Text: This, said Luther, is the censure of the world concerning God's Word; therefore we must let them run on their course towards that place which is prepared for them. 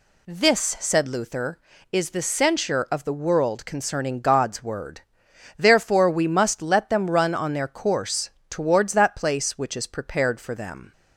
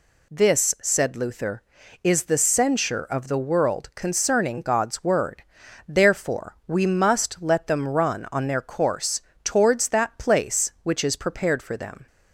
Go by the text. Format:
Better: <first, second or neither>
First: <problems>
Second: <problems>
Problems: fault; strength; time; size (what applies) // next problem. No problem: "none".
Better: neither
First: pauses between "course" and "towards"; slight; at 8.2 s; 0.20 s long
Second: pauses between "course" and "towards"; slight; at 9.2 s; 0.24 s long